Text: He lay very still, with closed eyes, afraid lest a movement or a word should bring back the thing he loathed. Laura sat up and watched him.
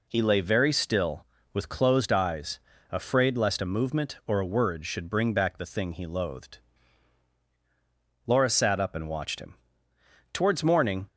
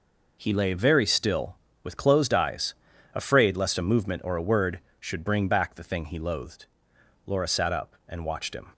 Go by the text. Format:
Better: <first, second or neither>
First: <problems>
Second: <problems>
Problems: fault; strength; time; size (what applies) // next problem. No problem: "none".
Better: second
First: goes on to say "Towards morning"; noticeable; from 10.3 s on; 0.76 s long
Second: none